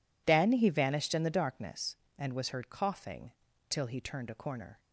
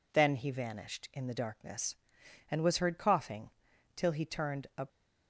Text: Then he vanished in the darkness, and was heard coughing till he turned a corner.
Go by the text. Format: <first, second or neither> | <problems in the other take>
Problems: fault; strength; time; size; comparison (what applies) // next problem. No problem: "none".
first | pauses between "coughing" and "till"; noticeable; at 3.4 s; 0.46 s long; slight in the first // stops before "corner"; at 4.8 s